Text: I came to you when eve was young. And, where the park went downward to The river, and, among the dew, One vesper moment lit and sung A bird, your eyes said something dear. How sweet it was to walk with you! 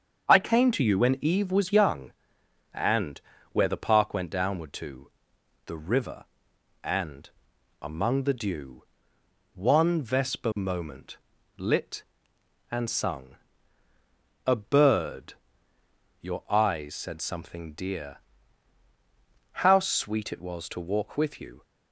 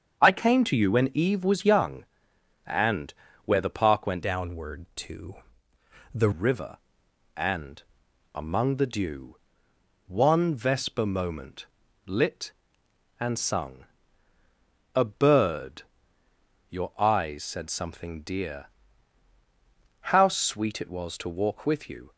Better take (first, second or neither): first